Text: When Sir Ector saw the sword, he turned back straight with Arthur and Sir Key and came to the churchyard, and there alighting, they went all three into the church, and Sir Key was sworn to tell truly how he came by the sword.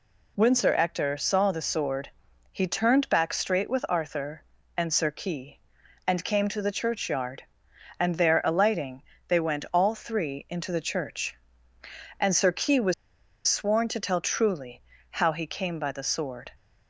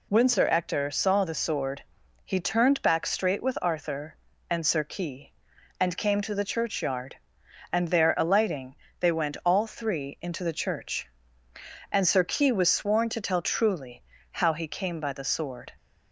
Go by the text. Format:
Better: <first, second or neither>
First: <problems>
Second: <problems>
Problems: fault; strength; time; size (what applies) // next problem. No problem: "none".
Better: second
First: pauses between "was" and "sworn"; noticeable; at 12.9 s; 0.53 s long // pauses between "truly" and "how"; slight; at 14.7 s; 0.30 s long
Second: pauses between "truly" and "how"; slight; at 14.0 s; 0.30 s long